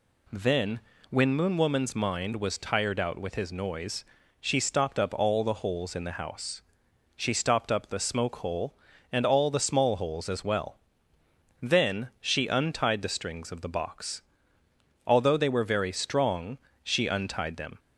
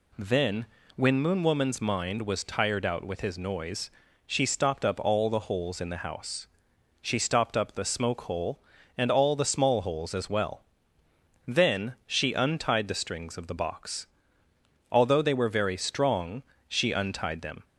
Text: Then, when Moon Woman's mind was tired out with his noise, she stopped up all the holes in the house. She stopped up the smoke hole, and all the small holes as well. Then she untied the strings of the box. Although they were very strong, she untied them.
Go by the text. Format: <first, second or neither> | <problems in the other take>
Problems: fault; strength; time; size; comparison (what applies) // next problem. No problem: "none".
neither | none